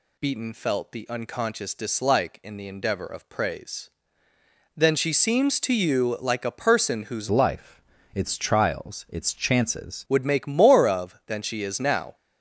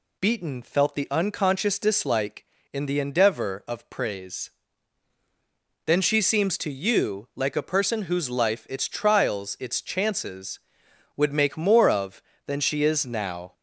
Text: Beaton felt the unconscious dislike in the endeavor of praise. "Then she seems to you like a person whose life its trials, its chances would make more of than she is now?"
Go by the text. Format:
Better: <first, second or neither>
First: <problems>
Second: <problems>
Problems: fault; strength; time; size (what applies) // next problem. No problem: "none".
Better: second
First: changes voice from "life" to "chances"; from 7.3 to 10.0 s; 2.7 s long // pauses between "life" and "its"; slight; at 7.8 s; 0.32 s long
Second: none